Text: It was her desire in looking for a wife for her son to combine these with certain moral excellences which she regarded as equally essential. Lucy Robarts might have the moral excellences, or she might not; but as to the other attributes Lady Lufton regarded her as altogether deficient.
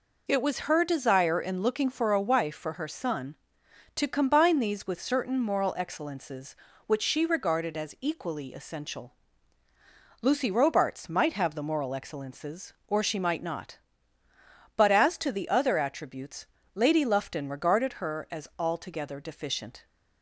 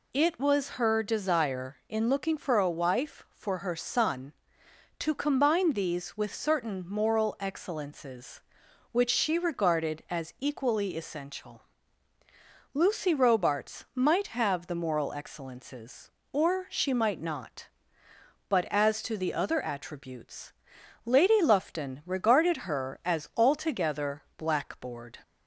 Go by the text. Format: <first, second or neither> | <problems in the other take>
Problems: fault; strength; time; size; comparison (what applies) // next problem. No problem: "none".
first | pauses between "attributes" and "Lady"; noticeable; at 20.5 s; 0.54 s long; slight in the first // says "blackboard" for "deficient"; at 24.3 s